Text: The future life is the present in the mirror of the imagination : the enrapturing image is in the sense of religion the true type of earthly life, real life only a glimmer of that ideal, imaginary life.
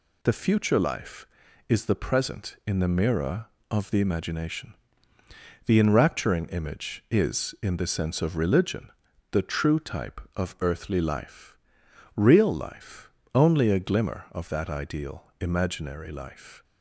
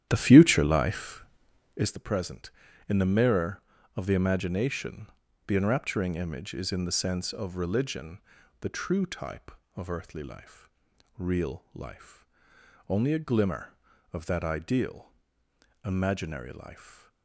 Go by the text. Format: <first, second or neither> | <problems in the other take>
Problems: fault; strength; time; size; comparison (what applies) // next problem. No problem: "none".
first | starts louder than the rest; strong; until 2.0 s; 11 dB // pauses between "religion" and "the"; at 8.2 s; 0.40 s long; also in the first // pauses between "life" and "only"; noticeable; at 12.2 s; 0.60 s long; slight in the first // stays silent after the last word; slight; from 16.7 s on; 0.5 s long